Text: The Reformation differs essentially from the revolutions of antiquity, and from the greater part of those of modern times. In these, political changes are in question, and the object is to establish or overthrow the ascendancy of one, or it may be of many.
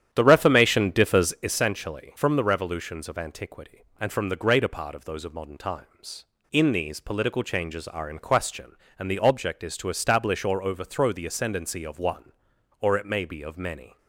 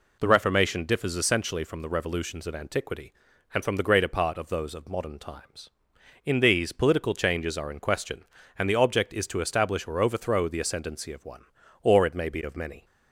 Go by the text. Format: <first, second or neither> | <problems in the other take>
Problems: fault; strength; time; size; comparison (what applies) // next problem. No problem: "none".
second | starts louder than the rest; strong; until 1.6 s; 10 dB